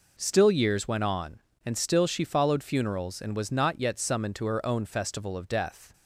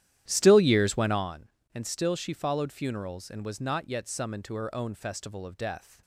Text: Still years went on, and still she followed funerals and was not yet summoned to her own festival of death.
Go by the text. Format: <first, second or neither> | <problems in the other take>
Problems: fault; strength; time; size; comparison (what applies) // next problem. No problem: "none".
first | starts louder than the rest; strong; until 1.3 s; 12 dB